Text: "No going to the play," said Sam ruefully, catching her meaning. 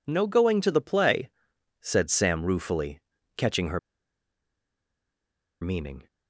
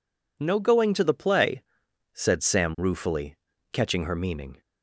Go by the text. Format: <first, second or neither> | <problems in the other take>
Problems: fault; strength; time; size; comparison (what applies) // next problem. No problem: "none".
second | pauses between "her" and "meaning"; strong; at 3.7 s; 1.8 s long